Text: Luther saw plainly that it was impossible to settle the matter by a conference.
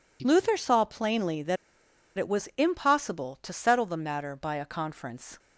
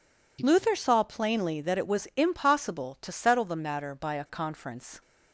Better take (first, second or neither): second